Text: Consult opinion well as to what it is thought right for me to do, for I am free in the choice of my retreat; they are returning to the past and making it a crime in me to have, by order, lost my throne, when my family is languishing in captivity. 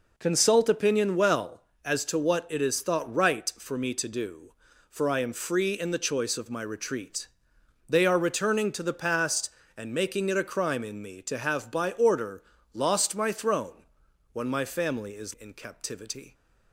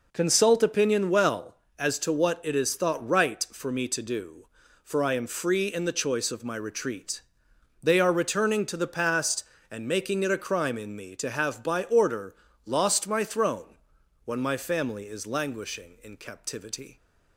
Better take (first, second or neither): second